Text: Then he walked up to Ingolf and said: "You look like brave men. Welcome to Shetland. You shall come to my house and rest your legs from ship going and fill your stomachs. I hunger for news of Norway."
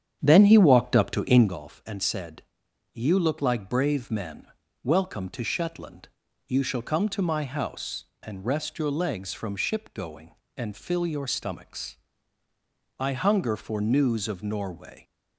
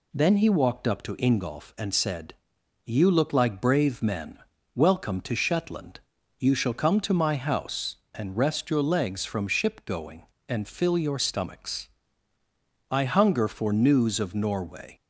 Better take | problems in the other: second | starts louder than the rest; strong; until 1.6 s; 8.5 dB

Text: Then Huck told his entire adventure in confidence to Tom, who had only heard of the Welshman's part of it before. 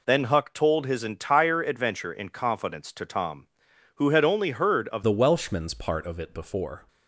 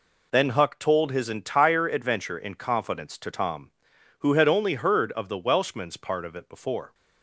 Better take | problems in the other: second | changes voice at "the"; from 5.0 s on; 1.8 s long

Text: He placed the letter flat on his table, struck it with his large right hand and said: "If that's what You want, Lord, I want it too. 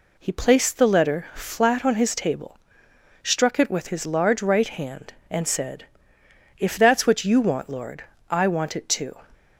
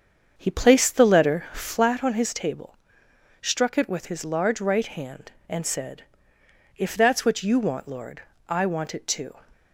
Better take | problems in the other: first | starts louder than the rest; strong; until 2.0 s; 7 dB

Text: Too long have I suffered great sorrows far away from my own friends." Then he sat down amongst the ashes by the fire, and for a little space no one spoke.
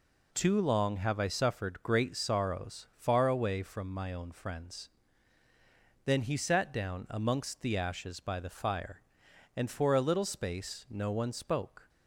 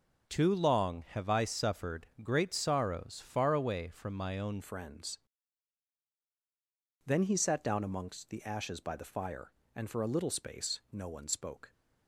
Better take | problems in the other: first | starts louder than the rest; until 1.3 s; 6.5 dB // changes voice at "friends"; from 4.6 s on; 7.1 s long

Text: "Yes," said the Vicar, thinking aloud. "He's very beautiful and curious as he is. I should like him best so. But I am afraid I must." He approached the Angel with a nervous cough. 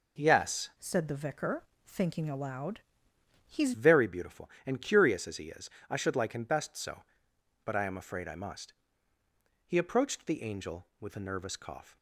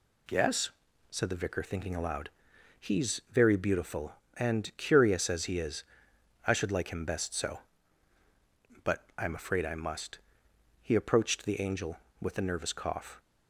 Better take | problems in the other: second | changes voice from "said" to "He's"; from 0.7 to 3.7 s; 3.0 s long

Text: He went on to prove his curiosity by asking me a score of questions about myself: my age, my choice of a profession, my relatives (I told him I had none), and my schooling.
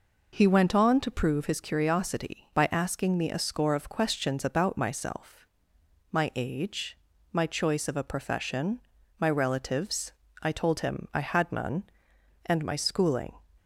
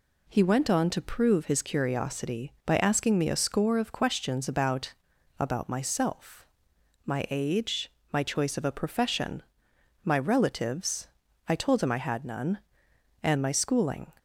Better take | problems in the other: first | says "about" twice; at 5.3 s

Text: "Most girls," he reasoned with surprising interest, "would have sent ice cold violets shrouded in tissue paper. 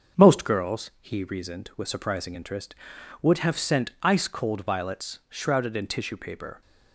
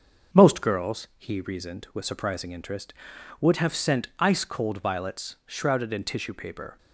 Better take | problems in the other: neither | starts louder than the rest; the same in both

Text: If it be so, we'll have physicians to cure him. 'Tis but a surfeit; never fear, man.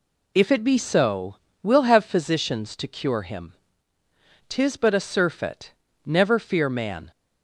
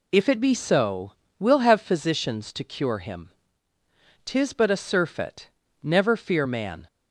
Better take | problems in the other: neither | none

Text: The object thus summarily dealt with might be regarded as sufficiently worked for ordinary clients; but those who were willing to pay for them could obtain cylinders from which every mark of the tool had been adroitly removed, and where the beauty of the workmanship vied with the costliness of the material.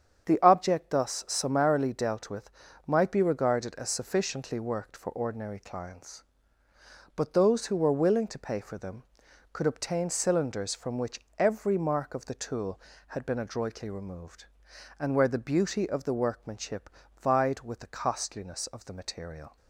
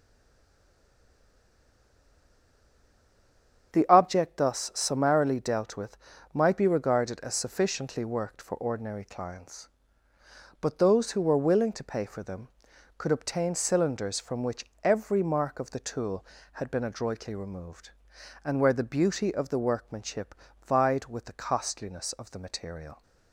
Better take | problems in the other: first | stays silent before the first word; strong; until 3.7 s; 3.7 s long // starts louder than the rest; strong; until 4.7 s; 8 dB; strong in the first // pauses between "with" and "might"; slight; at 5.9 s; 0.34 s long; slight in the first // pauses between "workmanship" and "vied"; slight; at 20.3 s; 0.28 s long; slight in the first

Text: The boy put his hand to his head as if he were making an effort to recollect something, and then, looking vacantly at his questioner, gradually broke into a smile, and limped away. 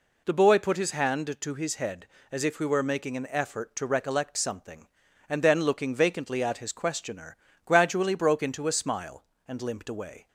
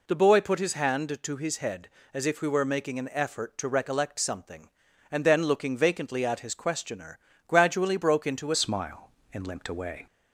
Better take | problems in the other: first | changes voice at "smile"; from 8.5 s on; 1.5 s long

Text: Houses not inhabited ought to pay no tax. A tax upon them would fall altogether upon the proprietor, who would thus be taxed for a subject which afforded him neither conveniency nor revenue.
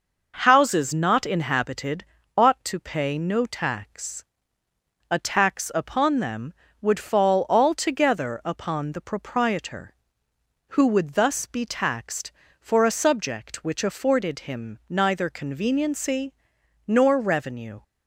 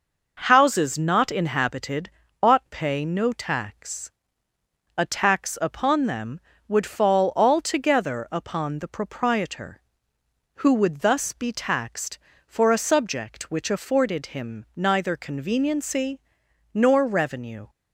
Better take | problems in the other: first | pauses between "inhabited" and "ought"; slight; at 2.0 s; 0.34 s long; slight in the first // skips "to"; at 2.6 s // pauses between "conveniency" and "nor"; noticeable; at 16.1 s; 0.56 s long; noticeable in the first

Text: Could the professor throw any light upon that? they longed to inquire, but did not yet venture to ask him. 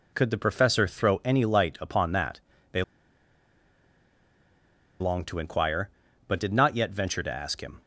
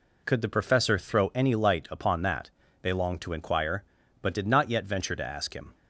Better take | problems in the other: second | pauses between "they" and "longed"; strong; at 2.8 s; 2.1 s long

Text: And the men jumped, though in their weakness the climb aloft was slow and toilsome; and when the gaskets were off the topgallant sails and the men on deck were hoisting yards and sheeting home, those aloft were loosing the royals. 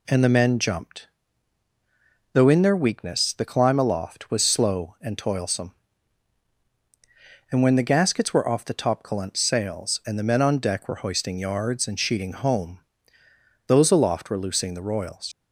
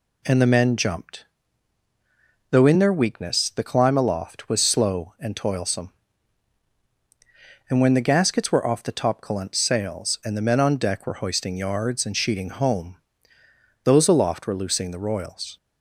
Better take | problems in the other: second | leaves "royals" unfinished; at 15.3 s; 80 ms

